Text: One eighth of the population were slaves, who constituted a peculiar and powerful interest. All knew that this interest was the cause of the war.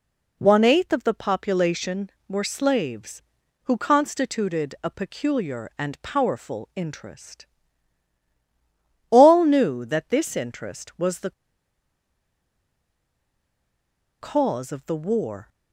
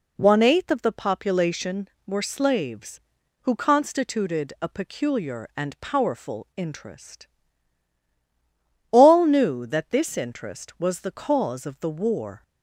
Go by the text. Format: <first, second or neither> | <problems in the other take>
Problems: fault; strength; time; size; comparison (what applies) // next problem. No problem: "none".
second | pauses between "the" and "cause"; strong; at 11.3 s; 2.8 s long